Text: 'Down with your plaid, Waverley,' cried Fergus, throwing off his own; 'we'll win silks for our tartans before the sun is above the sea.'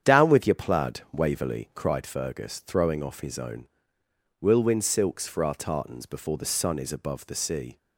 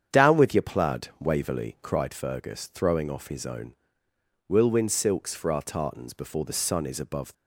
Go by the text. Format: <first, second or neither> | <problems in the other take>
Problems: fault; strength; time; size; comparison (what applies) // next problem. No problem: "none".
first | starts louder than the rest; strong; until 1.2 s; 8 dB; strong in the first // stops before "the sea"; at 7.3 s